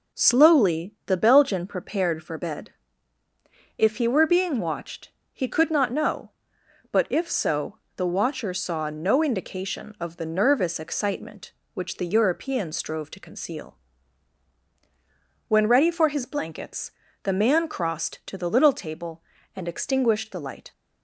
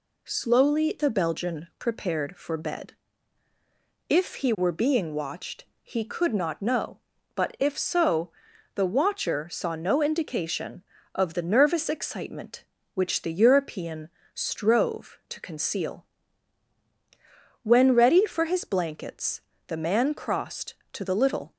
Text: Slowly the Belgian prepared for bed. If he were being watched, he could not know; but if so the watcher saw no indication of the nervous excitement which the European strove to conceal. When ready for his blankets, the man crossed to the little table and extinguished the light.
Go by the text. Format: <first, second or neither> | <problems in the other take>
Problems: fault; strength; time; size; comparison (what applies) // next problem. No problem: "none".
first | pauses between "so" and "the"; at 8.3 s; 0.44 s long; slight in the first // pauses between "European" and "strove"; slight; at 14.0 s; 0.26 s long // stops before "table and extinguished the light"; at 21.5 s